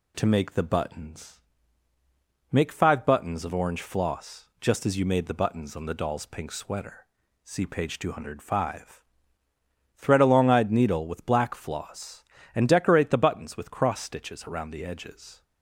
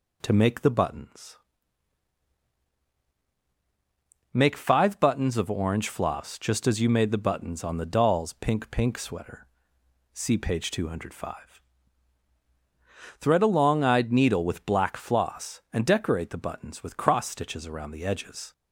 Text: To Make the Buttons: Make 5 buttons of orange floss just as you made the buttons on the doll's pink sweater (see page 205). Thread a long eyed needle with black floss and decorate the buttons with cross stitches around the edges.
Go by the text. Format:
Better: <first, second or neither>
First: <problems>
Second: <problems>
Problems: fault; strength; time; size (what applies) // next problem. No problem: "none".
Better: first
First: none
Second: says "pink" twice; at 8.7 s